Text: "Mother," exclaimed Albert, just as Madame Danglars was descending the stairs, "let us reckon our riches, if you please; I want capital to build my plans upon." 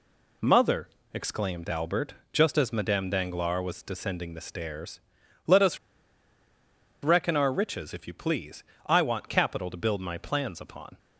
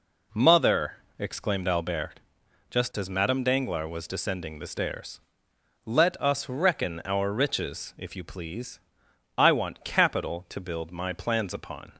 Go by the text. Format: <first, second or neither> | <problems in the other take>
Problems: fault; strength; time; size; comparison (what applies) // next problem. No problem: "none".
second | pauses between "us" and "reckon"; strong; at 5.7 s; 1.2 s long